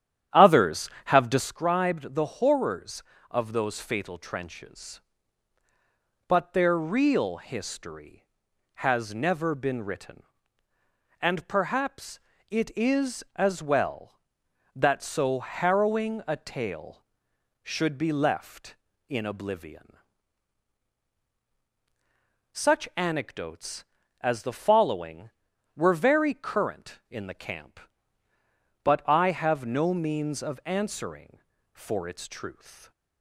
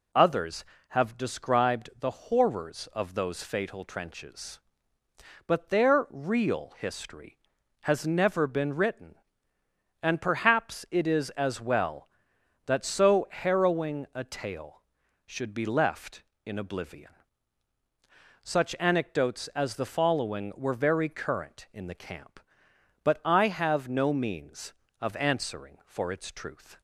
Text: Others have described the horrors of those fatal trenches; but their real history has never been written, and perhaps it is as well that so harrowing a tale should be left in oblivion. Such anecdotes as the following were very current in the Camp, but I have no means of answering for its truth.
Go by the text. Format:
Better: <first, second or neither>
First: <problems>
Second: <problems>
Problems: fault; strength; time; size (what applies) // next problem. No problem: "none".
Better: second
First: starts louder than the rest; strong; until 1.6 s; 10.5 dB // pauses between "perhaps" and "it"; slight; at 12.1 s; 0.30 s long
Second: none